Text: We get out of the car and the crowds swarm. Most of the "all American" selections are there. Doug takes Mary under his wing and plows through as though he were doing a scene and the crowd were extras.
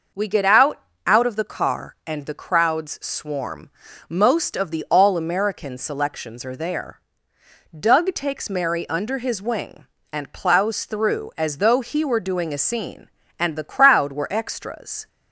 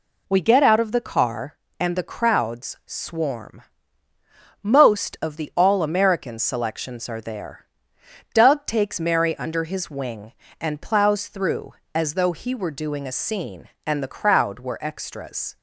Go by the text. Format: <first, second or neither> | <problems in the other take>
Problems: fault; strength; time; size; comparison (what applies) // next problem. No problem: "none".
second | says "out" twice; at 1.0 s